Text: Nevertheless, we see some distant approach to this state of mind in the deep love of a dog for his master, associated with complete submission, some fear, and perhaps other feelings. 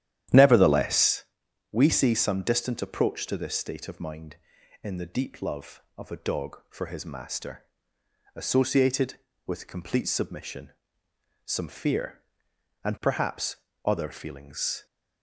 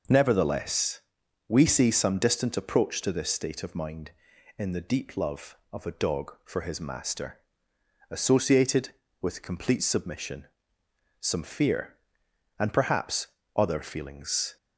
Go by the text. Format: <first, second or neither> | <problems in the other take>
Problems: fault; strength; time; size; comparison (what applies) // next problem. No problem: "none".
second | starts louder than the rest; strong; until 1.3 s; 11.5 dB // pauses between "perhaps" and "other"; slight; at 13.5 s; 0.28 s long; slight in the second